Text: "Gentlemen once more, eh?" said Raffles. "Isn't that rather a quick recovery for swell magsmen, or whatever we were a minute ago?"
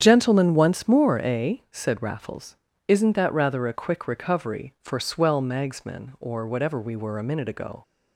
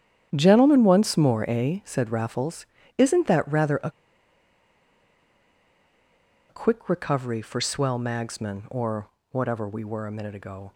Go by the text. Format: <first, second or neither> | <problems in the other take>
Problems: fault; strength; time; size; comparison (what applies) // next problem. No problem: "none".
first | starts louder than the rest; strong; until 1.3 s; 10 dB; strong in the first // pauses between "a" and "quick"; strong; at 3.8 s; 2.5 s long // pauses between "or" and "whatever"; slight; at 9.0 s; 0.22 s long